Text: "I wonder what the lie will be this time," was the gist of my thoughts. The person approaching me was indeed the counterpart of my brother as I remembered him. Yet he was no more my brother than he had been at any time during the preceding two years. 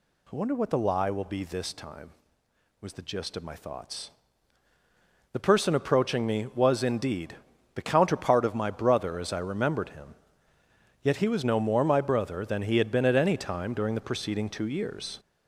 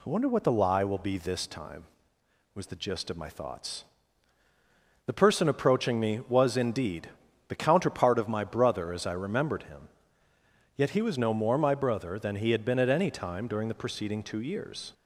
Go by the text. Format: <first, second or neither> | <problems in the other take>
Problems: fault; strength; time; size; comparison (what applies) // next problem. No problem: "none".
second | gets louder; noticeable; throughout; 5 dB // pauses between "indeed" and "the"; at 7.3 s; 0.40 s long; also in the second